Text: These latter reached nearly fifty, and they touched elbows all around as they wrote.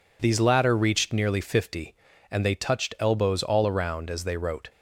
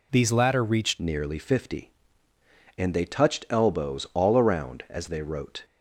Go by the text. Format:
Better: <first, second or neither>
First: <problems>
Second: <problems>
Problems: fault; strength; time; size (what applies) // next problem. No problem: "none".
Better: first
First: none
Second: changes voice at "nearly"; from 0.9 s on; 4.7 s long